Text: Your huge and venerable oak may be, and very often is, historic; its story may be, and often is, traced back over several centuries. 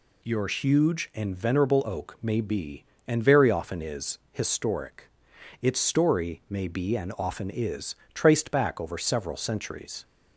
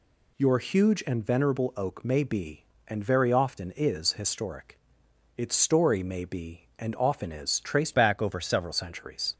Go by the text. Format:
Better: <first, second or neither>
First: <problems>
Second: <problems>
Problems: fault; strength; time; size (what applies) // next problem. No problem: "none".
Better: first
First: none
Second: changes voice from "back" to "several"; from 7.9 to 8.7 s; 0.8 s long